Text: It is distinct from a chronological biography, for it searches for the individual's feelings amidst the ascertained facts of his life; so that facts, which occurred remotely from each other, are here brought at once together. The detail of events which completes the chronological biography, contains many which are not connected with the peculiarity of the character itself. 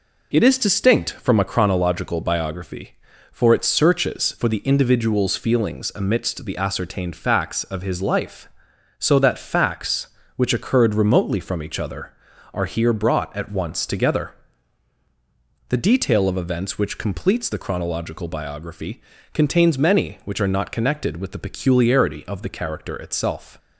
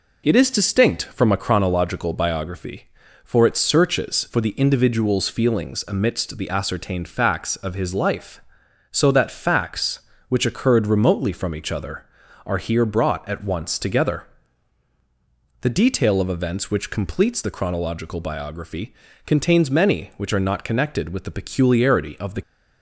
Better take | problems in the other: first | stops before "character itself"; at 22.4 s

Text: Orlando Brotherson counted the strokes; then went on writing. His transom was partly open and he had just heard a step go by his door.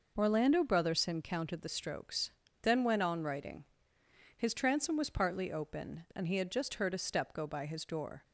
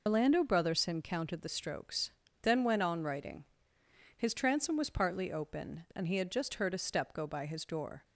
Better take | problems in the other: first | loses the start of "Orlando"; at 0.0 s; 110 ms

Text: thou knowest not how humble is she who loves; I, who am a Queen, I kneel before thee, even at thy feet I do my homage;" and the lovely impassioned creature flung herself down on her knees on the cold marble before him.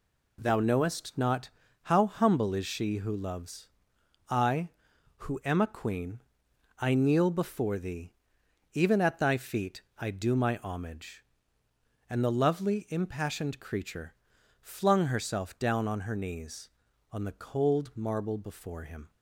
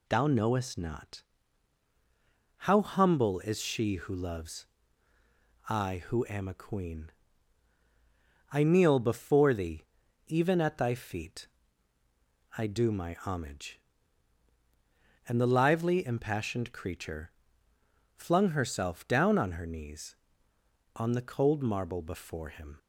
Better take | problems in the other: first | pauses between "not" and "how"; strong; at 1.2 s; 1.3 s long; slight in the first // pauses between "feet" and "I"; at 11.4 s; 1.1 s long; slight in the first // says "lively" for "lovely"; at 15.4 s // pauses between "creature" and "flung"; noticeable; at 17.2 s; 0.84 s long; also in the first

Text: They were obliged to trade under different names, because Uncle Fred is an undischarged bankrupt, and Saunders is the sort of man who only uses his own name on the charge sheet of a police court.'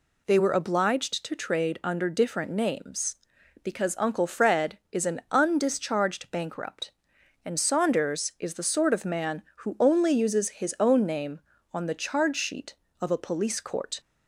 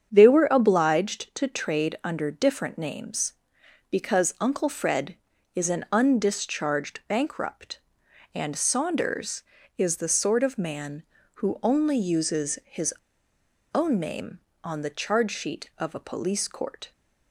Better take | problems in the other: first | starts louder than the rest; strong; until 1.1 s; 8 dB // pauses between "his" and "own"; noticeable; at 12.9 s; 0.79 s long

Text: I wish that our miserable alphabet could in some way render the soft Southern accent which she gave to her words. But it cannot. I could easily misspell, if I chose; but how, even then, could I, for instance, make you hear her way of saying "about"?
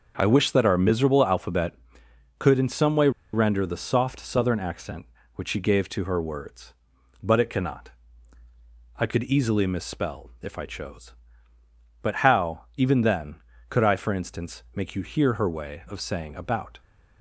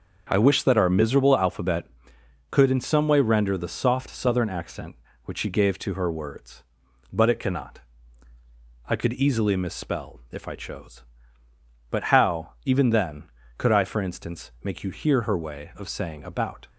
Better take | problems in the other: second | starts louder than the rest; until 1.2 s; 7 dB; also in the second // pauses between "way" and "render"; slight; at 3.0 s; 0.23 s long

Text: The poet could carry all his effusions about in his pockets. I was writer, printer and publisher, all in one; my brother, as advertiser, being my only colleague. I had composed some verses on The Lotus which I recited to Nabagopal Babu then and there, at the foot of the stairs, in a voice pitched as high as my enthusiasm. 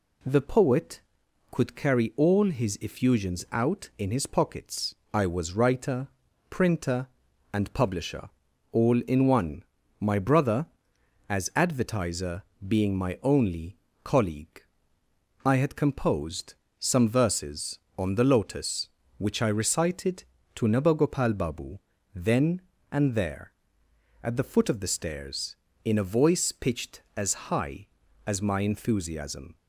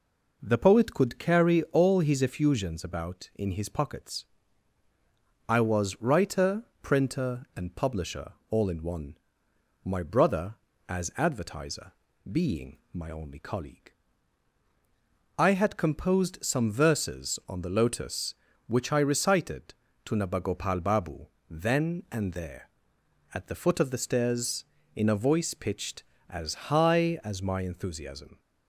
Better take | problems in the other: second | says "out" for "about"; at 3.5 s // pauses between "only" and "colleague"; slight; at 13.7 s; 0.26 s long // pauses between "composed" and "some"; slight; at 16.5 s; 0.26 s long // pauses between "Babu" and "then"; slight; at 21.7 s; 0.36 s long; slight in the second

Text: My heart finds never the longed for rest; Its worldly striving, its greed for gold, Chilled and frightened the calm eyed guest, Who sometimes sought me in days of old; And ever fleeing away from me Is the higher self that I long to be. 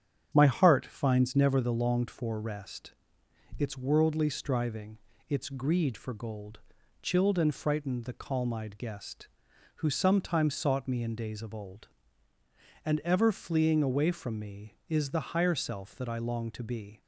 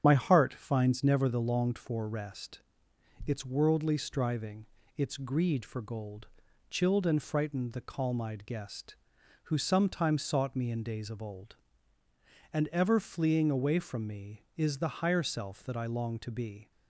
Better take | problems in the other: first | loses the start of "My"; at 0.0 s; 25 ms // starts louder than the rest; strong; until 1.0 s; 8.5 dB; strong in the first

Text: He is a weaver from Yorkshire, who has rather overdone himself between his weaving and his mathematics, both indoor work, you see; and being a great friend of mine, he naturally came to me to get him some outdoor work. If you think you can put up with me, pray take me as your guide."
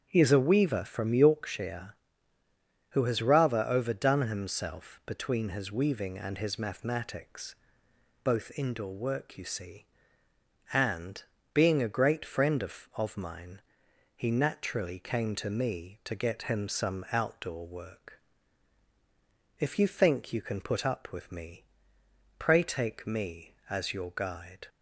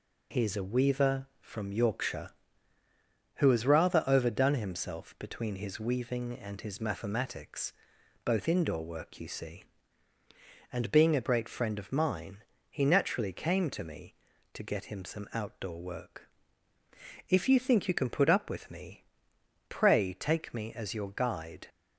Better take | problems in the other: second | starts louder than the rest; strong; until 1.1 s; 8 dB // pauses between "and" and "being"; slight; at 11.2 s; 0.32 s long // says "of" twice; at 12.9 s

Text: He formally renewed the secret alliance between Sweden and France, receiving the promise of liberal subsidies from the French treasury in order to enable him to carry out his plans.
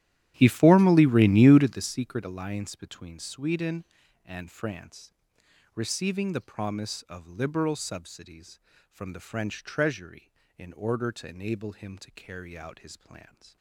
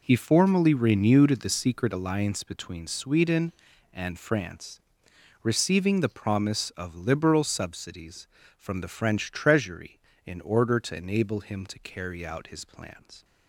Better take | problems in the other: second | starts louder than the rest; strong; until 1.9 s; 13 dB

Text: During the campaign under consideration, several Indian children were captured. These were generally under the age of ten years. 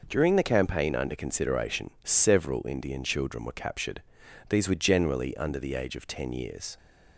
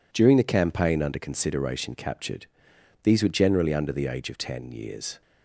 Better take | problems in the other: first | skips "several Indian children were"; at 1.9 s

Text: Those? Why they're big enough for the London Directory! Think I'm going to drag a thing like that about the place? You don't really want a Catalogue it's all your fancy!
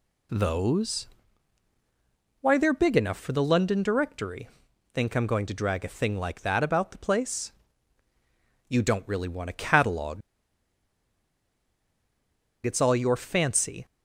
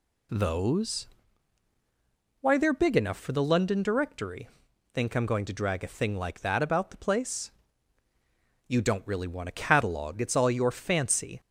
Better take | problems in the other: second | pauses between "Catalogue" and "it's"; strong; at 10.2 s; 2.4 s long

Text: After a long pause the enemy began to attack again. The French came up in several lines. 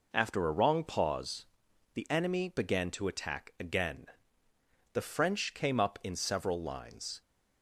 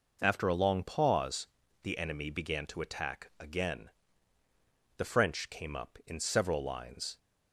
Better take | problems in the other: second | says "wrong" for "long"; at 0.5 s // pauses between "pause" and "the"; noticeable; at 1.4 s; 0.48 s long; slight in the second

